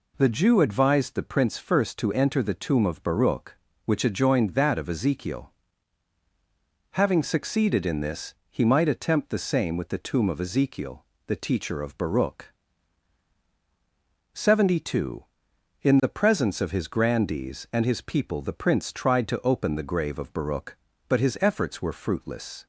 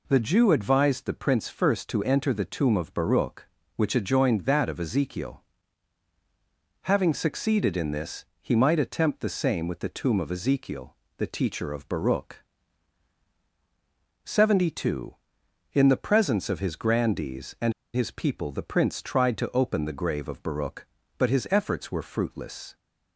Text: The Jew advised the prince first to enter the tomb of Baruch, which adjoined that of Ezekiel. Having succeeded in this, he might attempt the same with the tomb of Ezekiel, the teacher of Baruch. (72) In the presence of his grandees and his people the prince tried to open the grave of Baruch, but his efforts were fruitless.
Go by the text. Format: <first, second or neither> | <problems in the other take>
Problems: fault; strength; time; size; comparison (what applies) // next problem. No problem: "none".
first | pauses between "and" and "his"; slight; at 17.7 s; 0.22 s long